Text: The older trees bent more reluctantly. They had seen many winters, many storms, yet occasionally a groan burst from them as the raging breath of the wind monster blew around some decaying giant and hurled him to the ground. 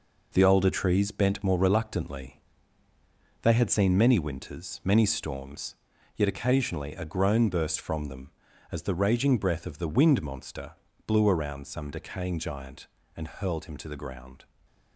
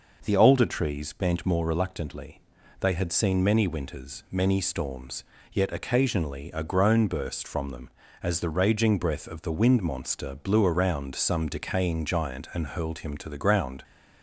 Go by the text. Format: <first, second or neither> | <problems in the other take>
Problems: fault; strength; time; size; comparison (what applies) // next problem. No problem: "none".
second | gets quieter; throughout; 7 dB // pauses between "monster" and "blew"; slight; at 10.7 s; 0.32 s long // stays silent after the last word; slight; from 14.4 s on; 0.5 s long